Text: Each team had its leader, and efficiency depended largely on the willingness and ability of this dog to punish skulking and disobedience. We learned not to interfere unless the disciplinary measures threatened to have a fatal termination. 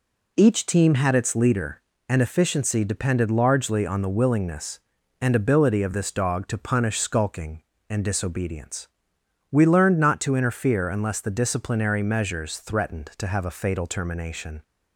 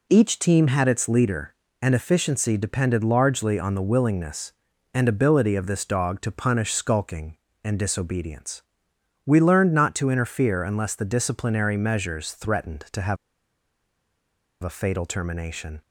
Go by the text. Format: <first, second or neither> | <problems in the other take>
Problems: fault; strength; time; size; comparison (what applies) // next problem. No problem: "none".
first | pauses between "have" and "a"; strong; at 13.1 s; 1.4 s long